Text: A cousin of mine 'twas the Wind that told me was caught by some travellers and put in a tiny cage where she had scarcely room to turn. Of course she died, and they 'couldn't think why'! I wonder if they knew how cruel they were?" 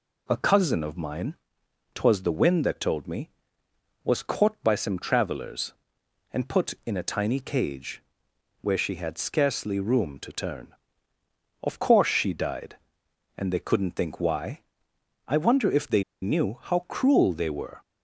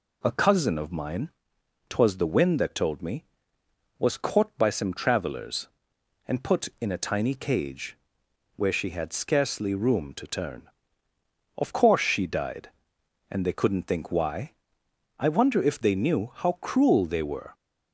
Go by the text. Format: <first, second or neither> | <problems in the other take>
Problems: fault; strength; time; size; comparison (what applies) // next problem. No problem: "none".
second | pauses between "mine" and "twas"; noticeable; at 1.3 s; 0.58 s long; noticeable in the second // pauses between "cage" and "where"; noticeable; at 8.0 s; 0.58 s long; noticeable in the second // pauses between "they" and "knew"; slight; at 16.0 s; 0.19 s long